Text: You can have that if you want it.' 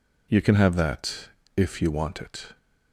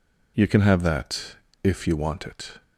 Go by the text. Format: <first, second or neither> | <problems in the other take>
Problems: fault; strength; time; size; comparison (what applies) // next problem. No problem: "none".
neither | pauses between "that" and "if"; slight; the same in both